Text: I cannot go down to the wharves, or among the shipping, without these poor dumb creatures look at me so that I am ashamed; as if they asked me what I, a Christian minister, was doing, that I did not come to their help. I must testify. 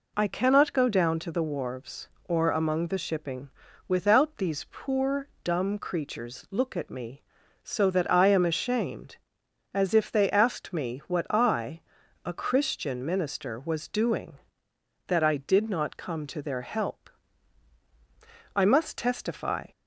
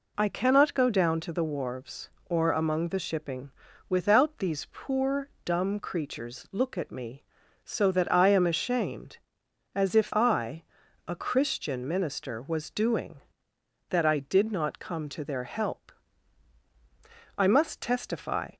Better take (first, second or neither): first